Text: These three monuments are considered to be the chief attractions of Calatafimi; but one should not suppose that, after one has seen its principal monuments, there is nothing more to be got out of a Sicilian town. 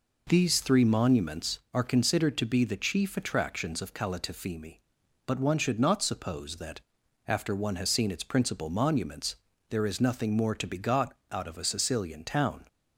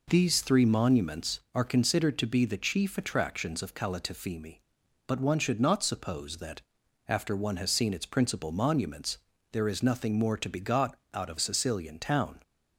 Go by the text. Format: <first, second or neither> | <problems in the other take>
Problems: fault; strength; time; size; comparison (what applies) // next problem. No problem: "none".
first | pauses between "got" and "out"; slight; at 10.9 s; 0.16 s long; slight in the first // skips "a"; at 11.3 s